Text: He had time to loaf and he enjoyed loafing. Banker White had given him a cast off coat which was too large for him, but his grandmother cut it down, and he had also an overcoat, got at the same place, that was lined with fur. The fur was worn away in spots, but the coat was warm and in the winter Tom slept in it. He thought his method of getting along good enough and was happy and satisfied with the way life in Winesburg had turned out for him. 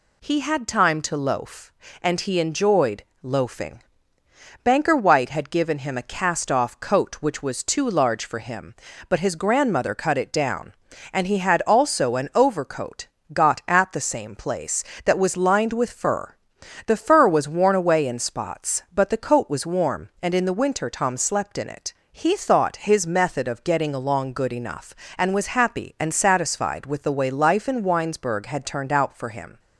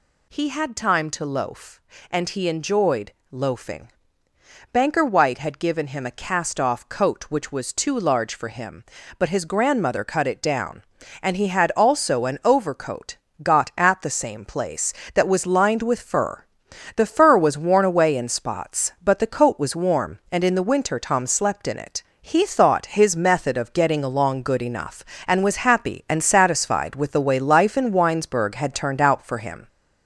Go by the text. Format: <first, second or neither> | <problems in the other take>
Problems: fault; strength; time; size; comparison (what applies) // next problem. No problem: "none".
first | gets louder; throughout; 4 dB // pauses between "enjoyed" and "loafing"; slight; at 3.1 s; 0.18 s long; slight in the first